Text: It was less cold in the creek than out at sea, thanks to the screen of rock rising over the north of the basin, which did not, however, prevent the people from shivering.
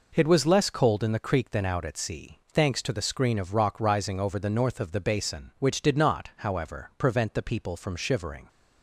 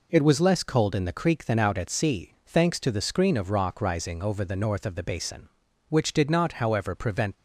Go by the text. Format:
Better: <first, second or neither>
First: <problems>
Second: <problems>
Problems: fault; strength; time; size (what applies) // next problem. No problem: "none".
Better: first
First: none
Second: stops before "the people from shivering"; at 7.3 s